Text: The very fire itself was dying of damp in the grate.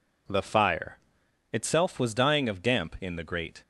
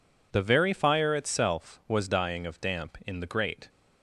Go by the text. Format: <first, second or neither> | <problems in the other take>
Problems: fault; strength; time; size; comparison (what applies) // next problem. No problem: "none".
second | skips "very"; at 0.4 s // pauses between "fire" and "itself"; noticeable; at 0.9 s; 0.54 s long